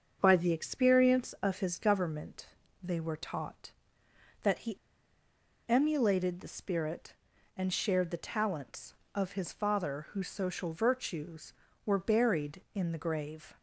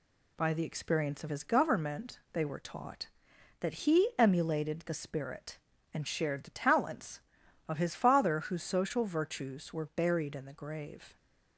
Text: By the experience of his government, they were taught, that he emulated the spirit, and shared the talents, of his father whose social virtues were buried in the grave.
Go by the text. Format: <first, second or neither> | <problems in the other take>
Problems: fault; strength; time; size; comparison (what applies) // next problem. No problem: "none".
second | starts louder than the rest; until 1.2 s; 6.5 dB // pauses between "he" and "emulated"; noticeable; at 4.7 s; 0.91 s long